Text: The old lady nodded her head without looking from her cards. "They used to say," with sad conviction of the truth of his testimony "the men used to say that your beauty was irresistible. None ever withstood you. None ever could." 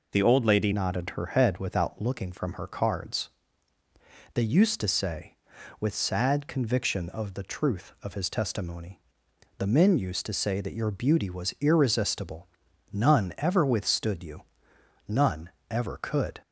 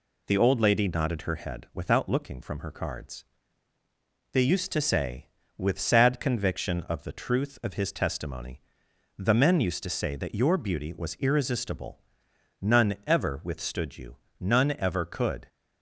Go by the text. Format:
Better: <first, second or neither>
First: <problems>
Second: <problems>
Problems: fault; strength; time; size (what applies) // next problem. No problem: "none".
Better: second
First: changes voice at "nodded"; from 0.7 s on; 15.7 s long // pauses between "testimony" and "the"; noticeable; at 9.0 s; 0.56 s long // pauses between "None" and "ever"; slight; at 15.4 s; 0.22 s long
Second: pauses between "testimony" and "the"; noticeable; at 8.6 s; 0.56 s long